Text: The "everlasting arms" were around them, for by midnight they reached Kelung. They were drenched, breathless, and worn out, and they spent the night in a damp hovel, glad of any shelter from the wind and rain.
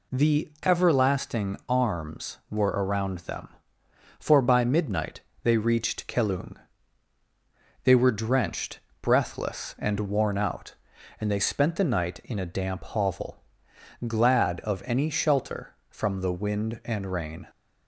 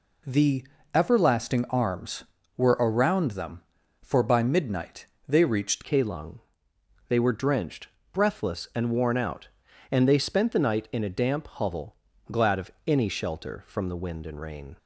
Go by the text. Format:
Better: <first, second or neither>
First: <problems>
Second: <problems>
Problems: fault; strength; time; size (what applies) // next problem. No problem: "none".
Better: first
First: pauses between "midnight" and "they"; slight; at 5.2 s; 0.22 s long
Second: pauses between "The" and "everlasting"; slight; at 0.6 s; 0.30 s long // pauses between "midnight" and "they"; slight; at 5.0 s; 0.22 s long // changes voice at "Kelung"; from 5.8 s on; 8.9 s long